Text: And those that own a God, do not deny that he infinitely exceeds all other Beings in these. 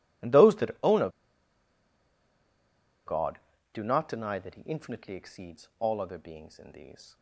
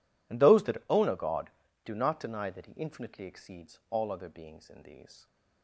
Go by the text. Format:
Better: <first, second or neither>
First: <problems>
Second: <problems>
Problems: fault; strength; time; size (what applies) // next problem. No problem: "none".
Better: second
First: pauses between "a" and "God"; strong; at 1.0 s; 1.9 s long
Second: none